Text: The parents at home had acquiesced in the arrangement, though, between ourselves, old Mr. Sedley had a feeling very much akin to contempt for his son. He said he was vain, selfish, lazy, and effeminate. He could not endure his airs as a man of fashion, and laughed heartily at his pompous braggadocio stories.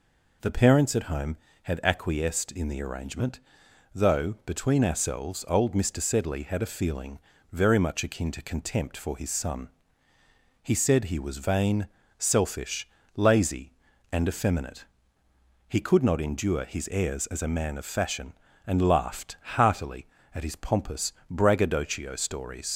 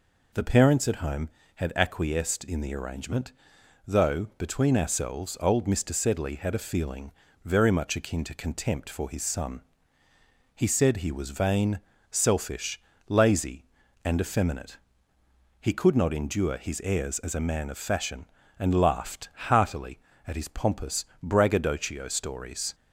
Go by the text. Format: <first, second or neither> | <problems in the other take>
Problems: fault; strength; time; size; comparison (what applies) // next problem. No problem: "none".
second | pauses between "feeling" and "very"; slight; at 7.1 s; 0.34 s long; slight in the second // pauses between "laughed" and "heartily"; slight; at 19.3 s; 0.20 s long; slight in the second // pauses between "pompous" and "braggadocio"; slight; at 21.1 s; 0.18 s long; slight in the second // leaves "stories" unfinished; at 22.7 s; 70 ms